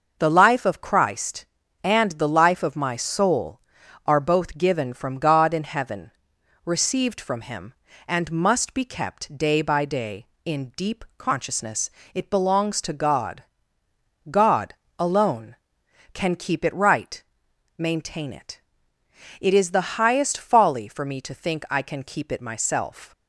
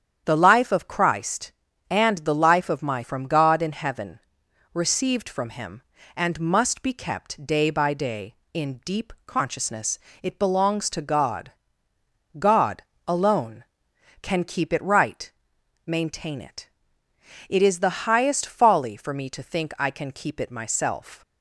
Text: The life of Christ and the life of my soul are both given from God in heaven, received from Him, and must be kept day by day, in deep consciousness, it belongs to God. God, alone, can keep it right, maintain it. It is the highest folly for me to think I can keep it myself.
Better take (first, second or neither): first